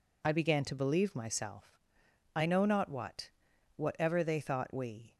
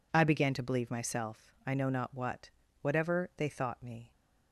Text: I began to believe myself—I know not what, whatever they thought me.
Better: second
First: says "we" for "me"; at 4.7 s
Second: none

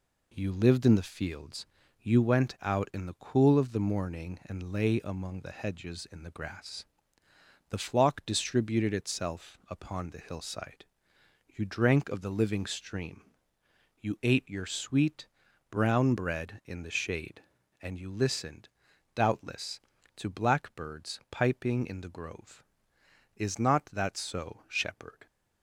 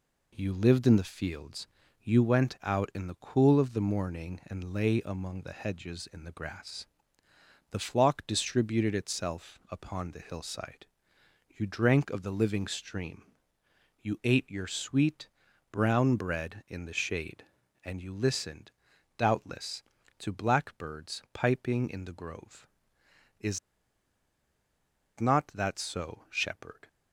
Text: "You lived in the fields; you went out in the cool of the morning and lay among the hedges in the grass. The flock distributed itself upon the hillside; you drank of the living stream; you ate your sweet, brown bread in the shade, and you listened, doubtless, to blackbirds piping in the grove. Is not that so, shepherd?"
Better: first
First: none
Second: pauses between "Is" and "not"; strong; at 23.5 s; 1.6 s long

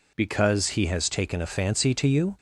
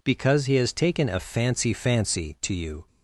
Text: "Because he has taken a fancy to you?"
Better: first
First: none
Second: says "fancy" twice; at 1.7 s

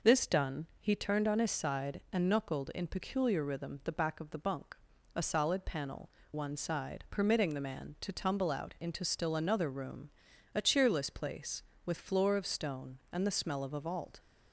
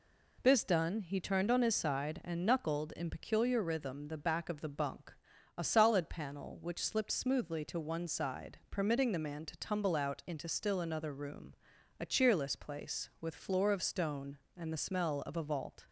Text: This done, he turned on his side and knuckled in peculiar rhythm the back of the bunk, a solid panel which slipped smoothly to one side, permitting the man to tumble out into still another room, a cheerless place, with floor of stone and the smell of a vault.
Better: second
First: skips "which slipped smoothly to"; at 6.2 s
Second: none

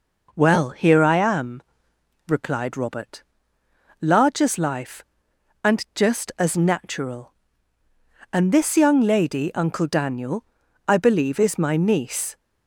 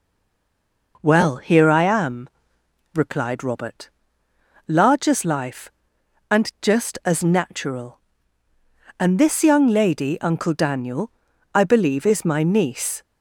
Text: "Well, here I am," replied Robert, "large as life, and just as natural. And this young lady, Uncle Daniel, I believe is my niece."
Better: first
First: none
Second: stays silent before the first word; slight; until 0.9 s; 0.9 s long

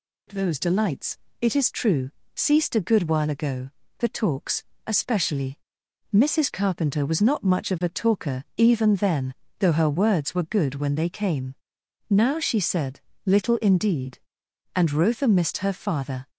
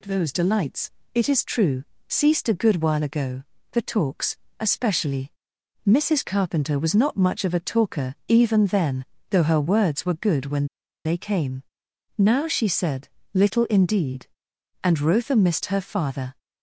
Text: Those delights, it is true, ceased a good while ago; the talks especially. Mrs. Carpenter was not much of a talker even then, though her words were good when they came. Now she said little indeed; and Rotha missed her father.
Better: first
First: pauses between "talks" and "especially"; slight; at 4.6 s; 0.22 s long // pauses between "said" and "little"; slight; at 12.9 s; 0.26 s long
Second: pauses between "talks" and "especially"; slight; at 4.3 s; 0.22 s long // pauses between "when" and "they"; at 10.6 s; 0.38 s long // pauses between "said" and "little"; slight; at 13.0 s; 0.26 s long

